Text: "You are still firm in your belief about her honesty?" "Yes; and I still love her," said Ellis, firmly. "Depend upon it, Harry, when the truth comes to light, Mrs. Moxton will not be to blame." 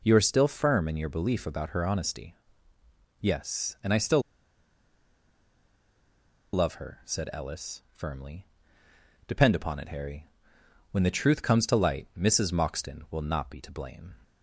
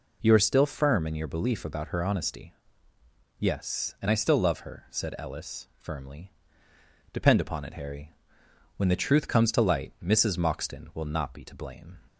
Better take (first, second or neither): second